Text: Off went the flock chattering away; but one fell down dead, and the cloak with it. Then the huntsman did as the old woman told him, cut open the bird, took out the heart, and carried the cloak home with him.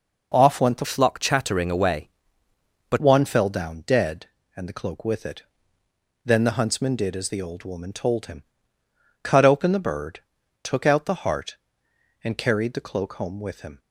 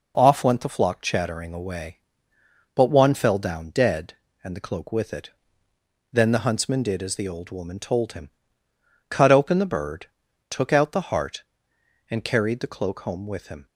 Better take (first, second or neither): second